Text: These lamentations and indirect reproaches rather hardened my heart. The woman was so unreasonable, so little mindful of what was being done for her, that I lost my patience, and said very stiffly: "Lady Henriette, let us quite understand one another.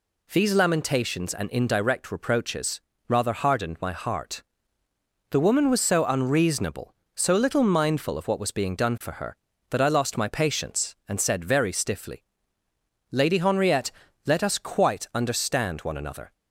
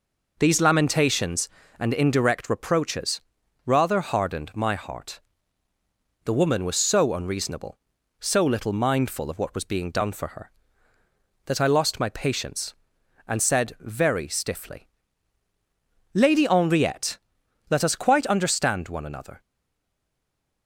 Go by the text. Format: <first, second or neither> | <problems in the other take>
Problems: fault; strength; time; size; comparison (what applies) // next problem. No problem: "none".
first | pauses between "reproaches" and "rather"; at 3.2 s; 0.44 s long; slight in the first // stays silent after the last word; noticeable; from 19.4 s on; 1.2 s long